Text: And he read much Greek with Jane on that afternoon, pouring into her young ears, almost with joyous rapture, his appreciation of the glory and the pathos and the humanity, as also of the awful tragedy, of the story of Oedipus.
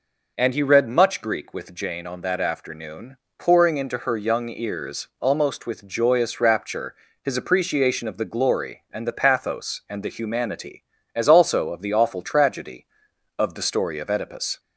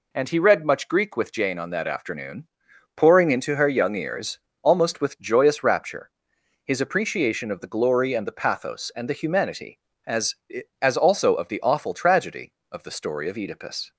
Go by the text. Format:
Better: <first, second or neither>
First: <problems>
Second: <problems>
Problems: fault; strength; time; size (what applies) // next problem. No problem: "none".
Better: first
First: none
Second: says "as" twice; at 10.8 s